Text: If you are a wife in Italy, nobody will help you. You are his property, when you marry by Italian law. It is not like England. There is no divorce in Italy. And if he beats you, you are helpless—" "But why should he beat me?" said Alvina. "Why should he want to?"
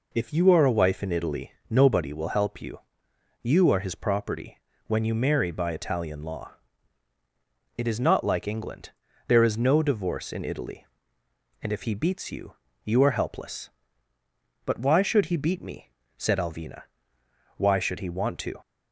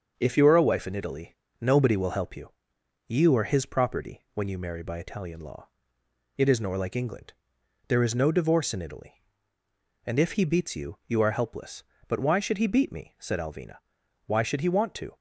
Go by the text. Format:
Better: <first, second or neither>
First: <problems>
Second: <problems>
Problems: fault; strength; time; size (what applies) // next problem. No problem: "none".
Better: first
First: none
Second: starts louder than the rest; until 1.1 s; 7 dB // says "nor" for "not"; at 6.6 s